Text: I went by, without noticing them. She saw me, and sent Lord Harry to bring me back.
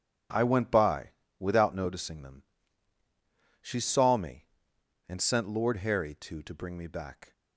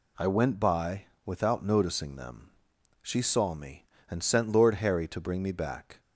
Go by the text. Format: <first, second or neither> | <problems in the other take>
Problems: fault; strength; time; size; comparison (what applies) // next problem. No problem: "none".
second | says "to" twice; at 6.4 s